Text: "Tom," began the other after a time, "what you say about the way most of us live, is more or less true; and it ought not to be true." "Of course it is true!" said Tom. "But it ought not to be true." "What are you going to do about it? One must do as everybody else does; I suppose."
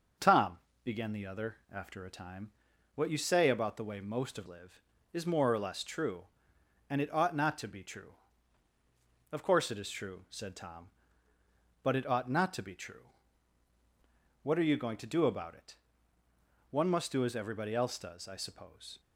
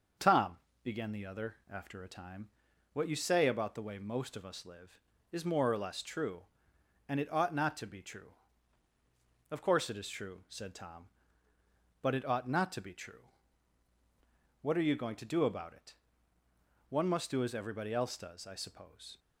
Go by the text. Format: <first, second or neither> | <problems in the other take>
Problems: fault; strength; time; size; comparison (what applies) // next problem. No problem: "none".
second | starts louder than the rest; until 1.4 s; 6 dB; also in the second // skips "us"; at 4.4 s